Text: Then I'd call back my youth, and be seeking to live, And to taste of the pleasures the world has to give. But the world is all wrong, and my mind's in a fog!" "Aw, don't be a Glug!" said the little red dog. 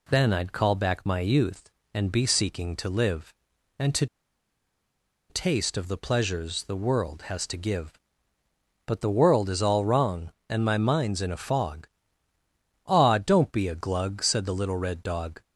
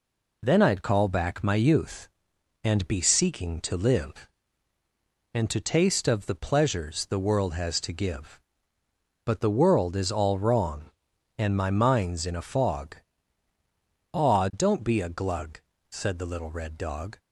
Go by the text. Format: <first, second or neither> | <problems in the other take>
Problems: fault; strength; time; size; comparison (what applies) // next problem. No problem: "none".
second | pauses between "to" and "taste"; at 4.0 s; 1.2 s long